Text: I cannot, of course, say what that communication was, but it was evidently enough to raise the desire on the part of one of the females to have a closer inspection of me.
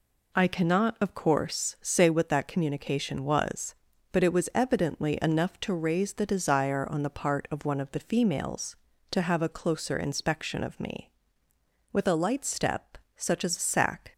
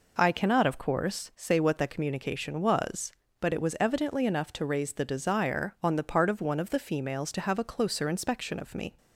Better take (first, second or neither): second